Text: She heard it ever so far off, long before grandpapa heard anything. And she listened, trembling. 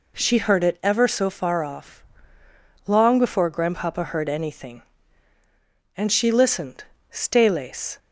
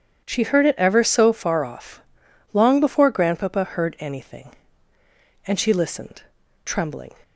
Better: second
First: says "staylace" for "trembling"; at 7.1 s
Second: none

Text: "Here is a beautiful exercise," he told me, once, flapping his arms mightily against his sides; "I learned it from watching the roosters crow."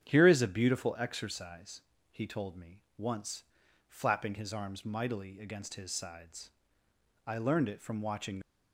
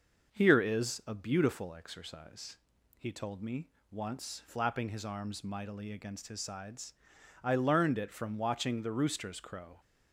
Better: second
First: starts louder than the rest; strong; until 1.0 s; 8.5 dB // stops before "the roosters crow"; at 8.4 s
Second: starts louder than the rest; until 1.4 s; 6 dB

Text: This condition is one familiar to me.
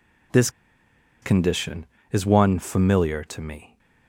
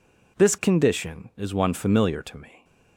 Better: second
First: pauses between "This" and "condition"; noticeable; at 0.4 s; 0.72 s long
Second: none

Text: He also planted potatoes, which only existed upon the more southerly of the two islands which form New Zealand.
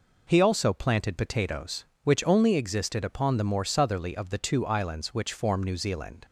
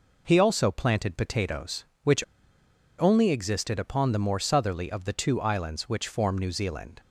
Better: first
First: none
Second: pauses between "which" and "only"; noticeable; at 2.2 s; 0.75 s long

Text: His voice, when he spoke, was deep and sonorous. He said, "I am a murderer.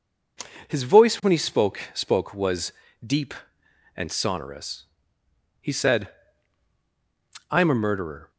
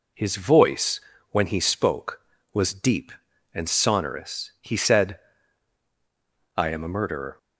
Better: second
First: says "spoke" twice; at 1.9 s // pauses between "was" and "deep"; slight; at 2.7 s; 0.32 s long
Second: none

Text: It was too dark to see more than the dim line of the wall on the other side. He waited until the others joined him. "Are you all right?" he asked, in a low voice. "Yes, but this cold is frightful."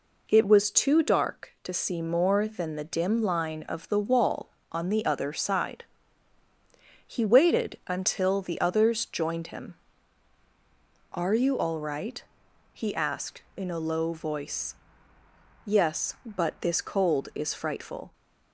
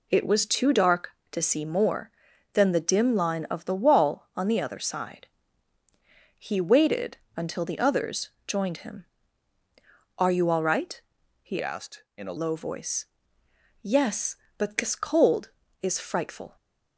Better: first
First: none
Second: pauses between "waited" and "until"; slight; at 7.1 s; 0.20 s long // pauses between "others" and "joined"; slight; at 8.2 s; 0.16 s long // changes voice from "asked" to "a"; from 11.6 to 12.3 s; 0.7 s long

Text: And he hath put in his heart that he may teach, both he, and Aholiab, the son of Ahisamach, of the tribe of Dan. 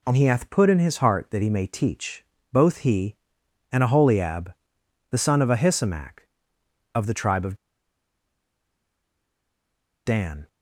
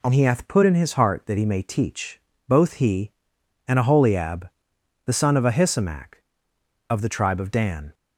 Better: second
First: pauses between "of" and "Dan"; strong; at 7.5 s; 2.5 s long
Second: none

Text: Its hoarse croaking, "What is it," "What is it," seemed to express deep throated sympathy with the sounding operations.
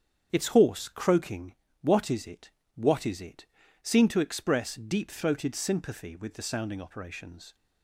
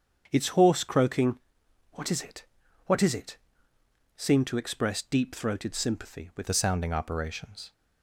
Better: first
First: starts louder than the rest; strong; until 1.3 s; 8 dB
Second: starts louder than the rest; strong; until 1.3 s; 7.5 dB // changes voice at "the"; from 6.4 s on; 1.3 s long

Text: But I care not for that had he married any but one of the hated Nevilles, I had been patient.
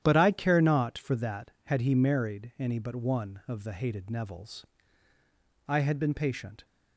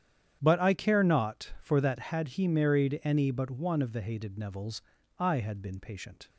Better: neither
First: starts louder than the rest; strong; until 1.0 s; 10.5 dB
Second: starts louder than the rest; strong; until 1.4 s; 9.5 dB

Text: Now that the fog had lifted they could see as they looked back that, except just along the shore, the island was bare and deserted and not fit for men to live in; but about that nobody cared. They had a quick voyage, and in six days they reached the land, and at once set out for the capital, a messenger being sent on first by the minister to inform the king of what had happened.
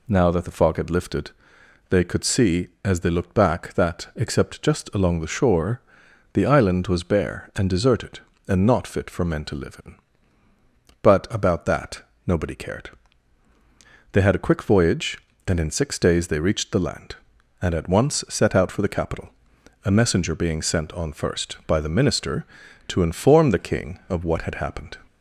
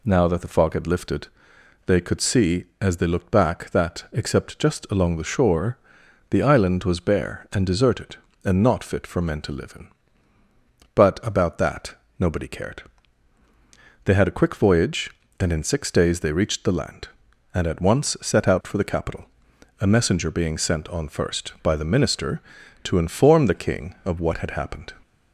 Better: neither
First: pauses between "lifted" and "they"; noticeable; at 1.3 s; 0.58 s long // pauses between "that" and "nobody"; slight; at 12.0 s; 0.24 s long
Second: pauses between "lifted" and "they"; noticeable; at 1.2 s; 0.58 s long // pauses between "that" and "nobody"; slight; at 11.9 s; 0.24 s long

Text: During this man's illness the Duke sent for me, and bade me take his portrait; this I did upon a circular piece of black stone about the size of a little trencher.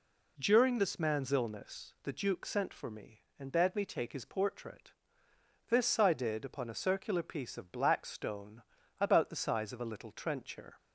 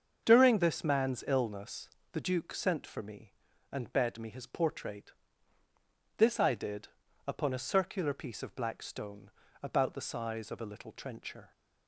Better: first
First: pauses between "stone" and "about"; at 8.6 s; 0.40 s long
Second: starts louder than the rest; until 1.2 s; 7 dB // pauses between "illness" and "the"; slight; at 1.8 s; 0.22 s long // skips "take"; at 4.2 s // pauses between "did" and "upon"; slight; at 6.8 s; 0.36 s long // pauses between "stone" and "about"; slight; at 9.3 s; 0.32 s long

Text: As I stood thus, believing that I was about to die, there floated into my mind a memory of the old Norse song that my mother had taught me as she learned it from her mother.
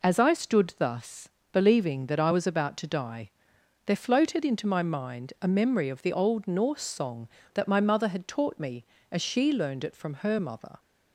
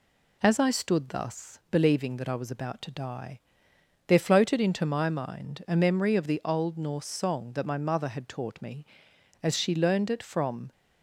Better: first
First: none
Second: stops before "her mother"; at 10.7 s

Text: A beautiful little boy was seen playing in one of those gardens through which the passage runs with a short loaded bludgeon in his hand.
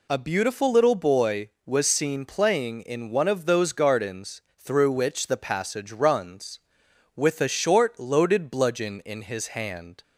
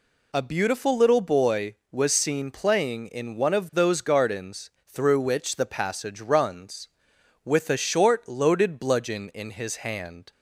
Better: neither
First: pauses between "gardens" and "through"; slight; at 4.4 s; 0.16 s long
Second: pauses between "gardens" and "through"; slight; at 4.7 s; 0.16 s long

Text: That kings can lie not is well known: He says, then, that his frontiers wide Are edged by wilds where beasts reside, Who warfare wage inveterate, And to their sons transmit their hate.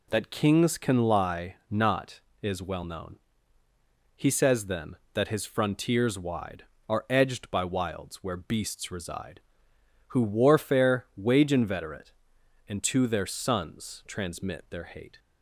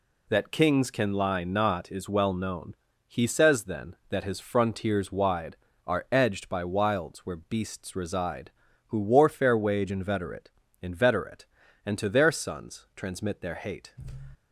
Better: first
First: none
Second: says "inveterate" twice; at 10.8 s

